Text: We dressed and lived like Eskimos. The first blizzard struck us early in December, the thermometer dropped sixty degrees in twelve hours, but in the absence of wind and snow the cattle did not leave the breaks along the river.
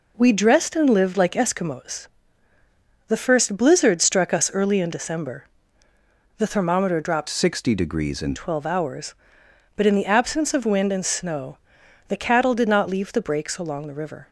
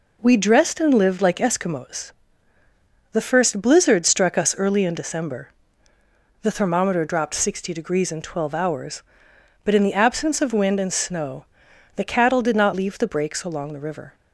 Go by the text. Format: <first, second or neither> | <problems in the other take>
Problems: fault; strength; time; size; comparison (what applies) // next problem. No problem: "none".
second | changes voice from "sixty" to "in"; from 7.2 to 8.3 s; 1.1 s long // pauses between "snow" and "the"; noticeable; at 11.5 s; 0.50 s long; noticeable in the second